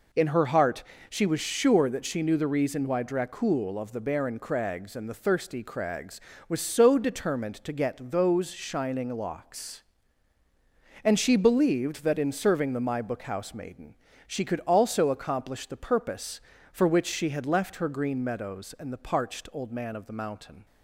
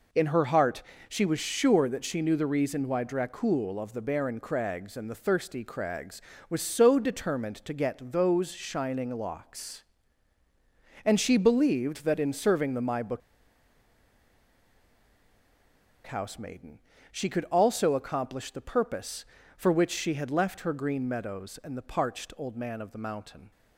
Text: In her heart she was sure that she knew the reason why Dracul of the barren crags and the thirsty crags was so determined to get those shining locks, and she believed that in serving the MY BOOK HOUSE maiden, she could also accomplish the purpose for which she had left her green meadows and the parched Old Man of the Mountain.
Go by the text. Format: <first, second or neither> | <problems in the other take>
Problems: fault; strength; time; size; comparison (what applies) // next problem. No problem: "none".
first | pauses between "heart" and "she"; slight; at 0.8 s; 0.26 s long; slight in the first // pauses between "BOOK" and "HOUSE"; strong; at 13.2 s; 2.8 s long